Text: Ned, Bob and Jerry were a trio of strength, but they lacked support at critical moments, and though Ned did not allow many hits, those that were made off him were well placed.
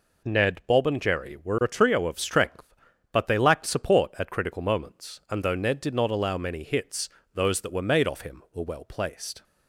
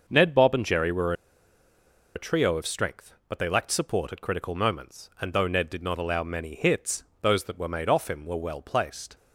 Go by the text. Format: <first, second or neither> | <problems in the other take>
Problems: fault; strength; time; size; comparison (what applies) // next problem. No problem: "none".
first | starts louder than the rest; noticeable; until 1.0 s; 6 dB // pauses between "were" and "a"; at 1.1 s; 1.0 s long